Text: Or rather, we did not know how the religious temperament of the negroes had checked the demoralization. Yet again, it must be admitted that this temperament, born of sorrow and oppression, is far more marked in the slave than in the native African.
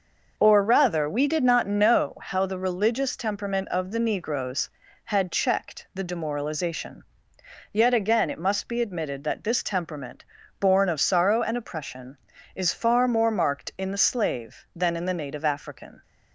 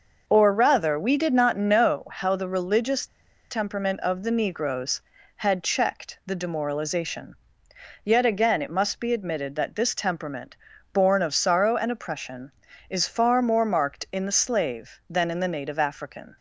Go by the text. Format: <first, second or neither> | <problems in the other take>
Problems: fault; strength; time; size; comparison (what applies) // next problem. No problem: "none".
first | pauses between "religious" and "temperament"; at 3.0 s; 0.44 s long